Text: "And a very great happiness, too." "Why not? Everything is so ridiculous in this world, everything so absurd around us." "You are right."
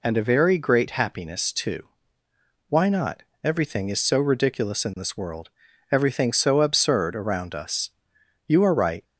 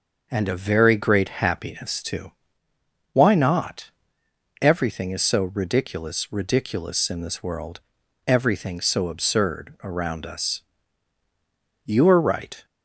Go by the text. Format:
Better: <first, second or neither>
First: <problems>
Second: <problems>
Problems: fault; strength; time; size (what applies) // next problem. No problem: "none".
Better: first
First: none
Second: starts louder than the rest; noticeable; until 1.3 s; 6 dB // says "ridiculous" twice; at 6.3 s